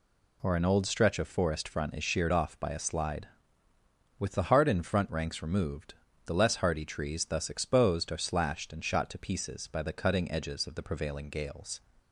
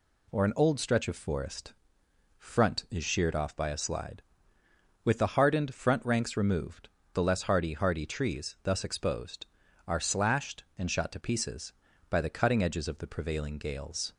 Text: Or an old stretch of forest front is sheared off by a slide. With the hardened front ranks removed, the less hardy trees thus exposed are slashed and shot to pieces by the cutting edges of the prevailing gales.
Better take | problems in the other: first | pauses between "forest" and "front"; noticeable; at 1.7 s; 0.64 s long // says "hardy" twice; at 7.7 s

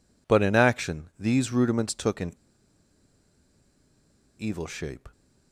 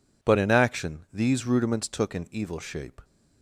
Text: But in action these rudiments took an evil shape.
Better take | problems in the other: second | pauses between "an" and "evil"; strong; at 2.3 s; 2.0 s long

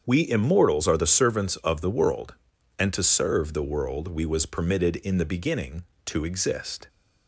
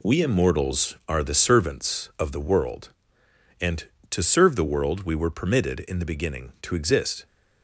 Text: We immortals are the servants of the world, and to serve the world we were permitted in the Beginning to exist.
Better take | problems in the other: second | starts louder than the rest; strong; until 1.0 s; 7.5 dB // says "was" for "were"; at 4.2 s

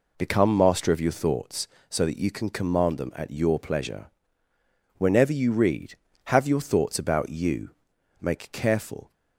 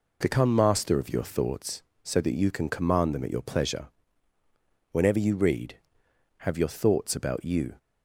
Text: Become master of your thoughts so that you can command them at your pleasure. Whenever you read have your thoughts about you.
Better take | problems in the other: second | goes on to say "Make careful"; noticeable; from 8.2 s on; 0.92 s long

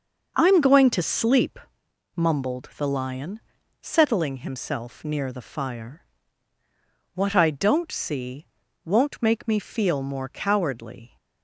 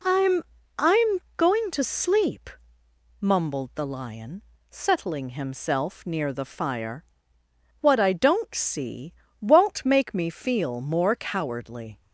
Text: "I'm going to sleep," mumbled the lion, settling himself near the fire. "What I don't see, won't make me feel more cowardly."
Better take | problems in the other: first | says "I'm" twice; at 0.8 s

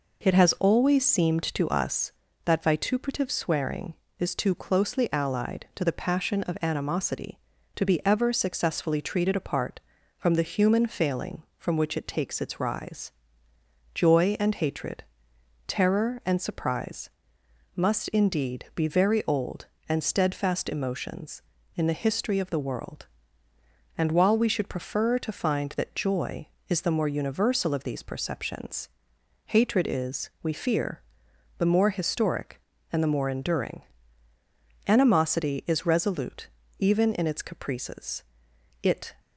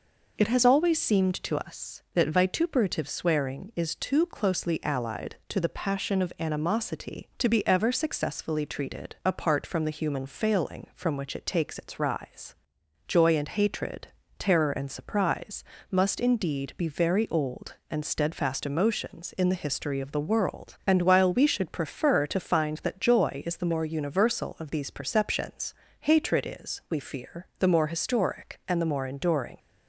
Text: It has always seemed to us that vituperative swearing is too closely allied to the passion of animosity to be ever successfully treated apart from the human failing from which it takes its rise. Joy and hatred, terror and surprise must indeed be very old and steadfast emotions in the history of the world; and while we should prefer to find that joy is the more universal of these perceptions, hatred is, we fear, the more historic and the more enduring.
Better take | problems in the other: second | pauses between "surprise" and "must"; noticeable; at 17.0 s; 0.66 s long; slight in the second // goes on to say "Animosity is resolute even in its caprices it"; strong; from 34.8 s on; 4.2 s long

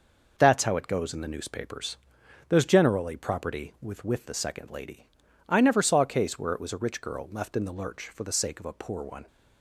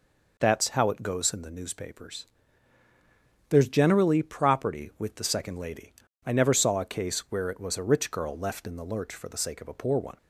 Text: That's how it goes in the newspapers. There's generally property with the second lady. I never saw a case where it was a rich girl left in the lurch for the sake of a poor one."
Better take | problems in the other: second | says "with" twice; at 4.0 s

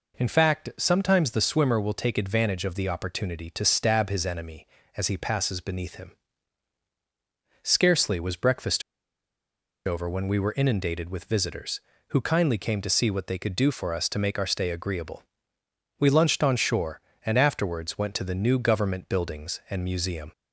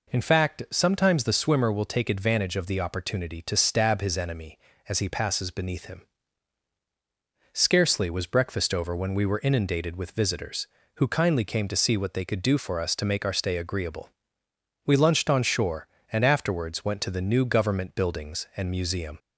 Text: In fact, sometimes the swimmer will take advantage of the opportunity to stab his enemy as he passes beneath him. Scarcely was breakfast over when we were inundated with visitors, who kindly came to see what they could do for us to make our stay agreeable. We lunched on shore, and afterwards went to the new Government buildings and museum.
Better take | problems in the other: second | pauses between "breakfast" and "over"; at 8.8 s; 1.0 s long

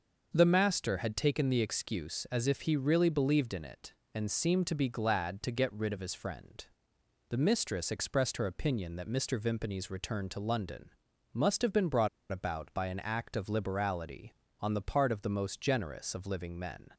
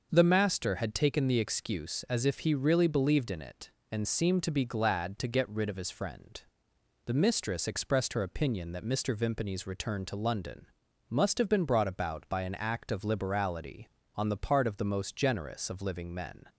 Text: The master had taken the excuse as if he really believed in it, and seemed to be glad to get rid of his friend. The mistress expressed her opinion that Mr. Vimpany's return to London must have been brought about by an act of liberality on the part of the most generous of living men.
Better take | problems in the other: second | starts louder than the rest; until 1.3 s; 6 dB; also in the second // pauses between "London" and "must"; noticeable; at 10.8 s; 0.46 s long; noticeable in the second // pauses between "brought" and "about"; slight; at 12.0 s; 0.22 s long

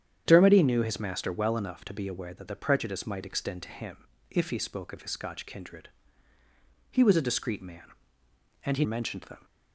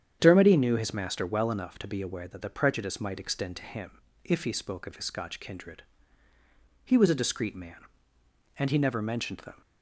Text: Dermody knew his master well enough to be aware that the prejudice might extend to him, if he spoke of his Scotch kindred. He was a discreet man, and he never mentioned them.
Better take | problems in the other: second | starts louder than the rest; strong; until 1.2 s; 9 dB; strong in the second // skips "never"; at 8.8 s

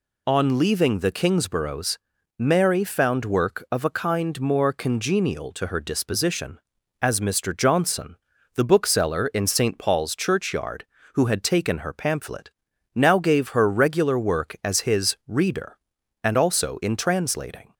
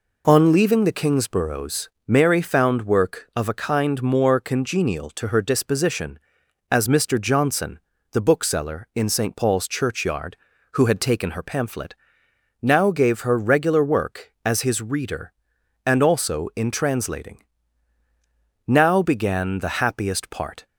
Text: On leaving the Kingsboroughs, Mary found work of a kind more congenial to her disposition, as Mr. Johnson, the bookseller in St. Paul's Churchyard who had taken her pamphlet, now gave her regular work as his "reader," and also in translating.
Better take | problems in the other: first | goes on to say "Now began the happiest part"; strong; from 18.6 s on; 1.9 s long

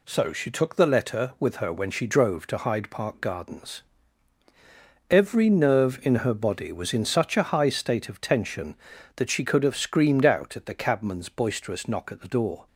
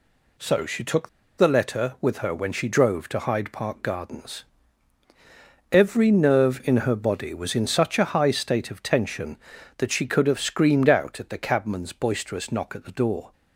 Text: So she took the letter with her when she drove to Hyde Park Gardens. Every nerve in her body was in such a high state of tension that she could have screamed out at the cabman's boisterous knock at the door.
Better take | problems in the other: first | pauses between "took" and "the"; slight; at 1.0 s; 0.28 s long

